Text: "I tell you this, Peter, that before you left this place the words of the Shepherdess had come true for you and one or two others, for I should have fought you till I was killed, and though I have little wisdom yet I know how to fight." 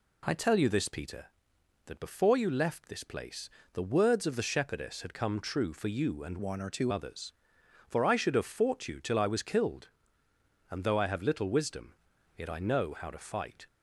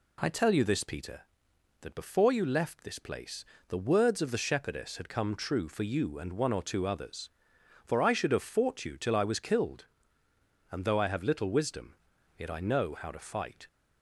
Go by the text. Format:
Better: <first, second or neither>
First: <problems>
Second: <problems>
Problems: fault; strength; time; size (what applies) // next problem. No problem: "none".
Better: second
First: pauses between "place" and "the"; slight; at 3.4 s; 0.24 s long // changes voice from "one" to "two"; from 6.3 to 6.9 s; 0.6 s long // pauses between "wisdom" and "yet"; at 11.9 s; 0.42 s long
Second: pauses between "place" and "the"; slight; at 3.4 s; 0.24 s long // pauses between "wisdom" and "yet"; at 11.9 s; 0.42 s long